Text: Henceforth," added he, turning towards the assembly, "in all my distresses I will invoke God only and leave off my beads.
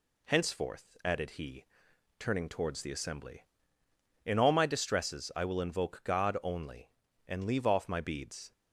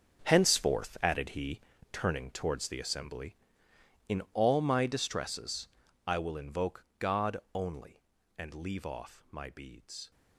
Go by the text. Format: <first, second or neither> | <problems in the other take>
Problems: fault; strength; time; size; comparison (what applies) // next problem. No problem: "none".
first | gets quieter; strong; throughout; 14 dB // pauses between "distresses" and "I"; at 5.6 s; 0.38 s long // pauses between "God" and "only"; slight; at 7.3 s; 0.16 s long